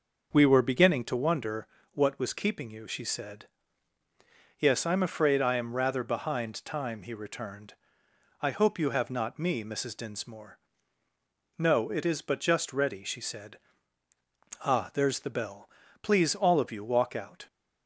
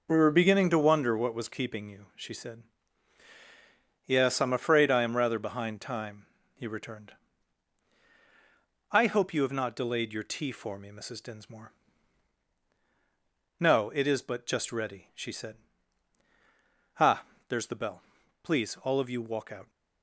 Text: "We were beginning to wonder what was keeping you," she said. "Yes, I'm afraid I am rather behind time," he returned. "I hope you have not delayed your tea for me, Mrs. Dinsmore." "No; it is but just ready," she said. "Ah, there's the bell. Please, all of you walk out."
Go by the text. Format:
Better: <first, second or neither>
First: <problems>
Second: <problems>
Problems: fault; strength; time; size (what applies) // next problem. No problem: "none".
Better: second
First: starts louder than the rest; until 1.3 s; 6 dB // pauses between "wonder" and "what"; slight; at 1.6 s; 0.26 s long // skips "delayed your tea for"; at 9.3 s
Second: none